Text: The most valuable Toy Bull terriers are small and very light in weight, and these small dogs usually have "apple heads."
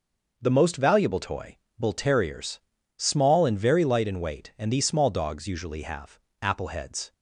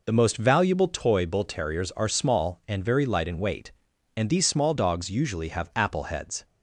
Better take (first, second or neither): second